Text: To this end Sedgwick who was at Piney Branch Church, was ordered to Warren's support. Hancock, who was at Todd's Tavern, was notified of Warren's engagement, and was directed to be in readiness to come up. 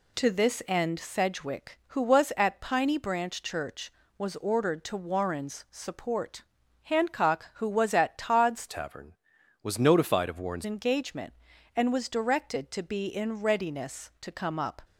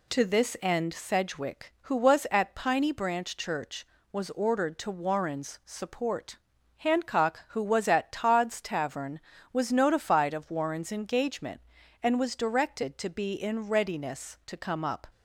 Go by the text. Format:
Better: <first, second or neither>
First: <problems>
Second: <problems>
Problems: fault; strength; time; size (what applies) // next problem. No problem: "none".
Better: second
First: changes voice from "Tavern" to "Warren's"; from 8.6 to 10.6 s; 2.0 s long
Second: none